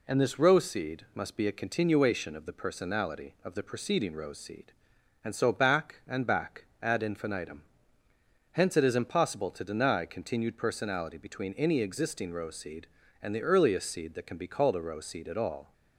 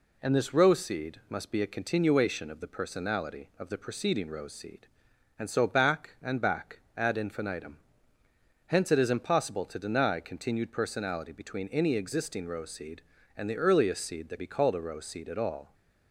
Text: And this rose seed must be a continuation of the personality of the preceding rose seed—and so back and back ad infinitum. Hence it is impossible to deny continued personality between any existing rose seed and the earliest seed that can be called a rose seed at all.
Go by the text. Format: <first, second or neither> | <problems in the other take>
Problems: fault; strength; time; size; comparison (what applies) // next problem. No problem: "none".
first | pauses between "back" and "ad"; slight; at 6.8 s; 0.16 s long; slight in the first // skips "can"; at 14.3 s